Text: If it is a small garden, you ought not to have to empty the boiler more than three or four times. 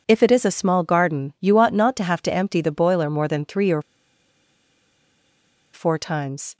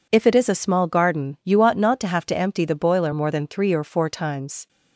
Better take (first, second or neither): second